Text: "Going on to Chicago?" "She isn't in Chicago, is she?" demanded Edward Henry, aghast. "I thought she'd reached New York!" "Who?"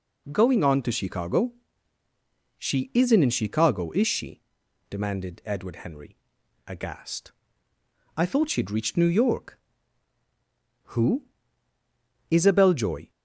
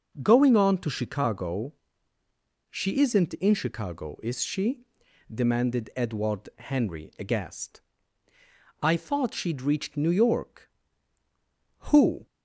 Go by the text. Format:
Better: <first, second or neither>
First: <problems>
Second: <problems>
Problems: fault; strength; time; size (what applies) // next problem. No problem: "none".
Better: second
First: goes on to say "Isabel Joy"; noticeable; from 12.2 s on; 0.80 s long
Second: none